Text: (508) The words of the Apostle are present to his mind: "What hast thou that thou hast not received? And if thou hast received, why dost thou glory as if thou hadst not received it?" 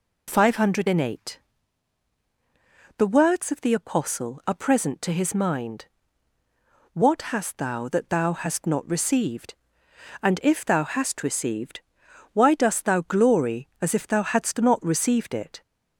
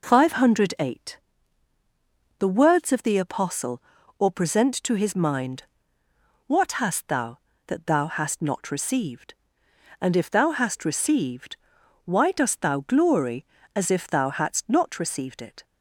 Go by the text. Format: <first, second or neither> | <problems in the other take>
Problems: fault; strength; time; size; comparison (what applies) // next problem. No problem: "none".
first | says "or" for "are"; at 4.1 s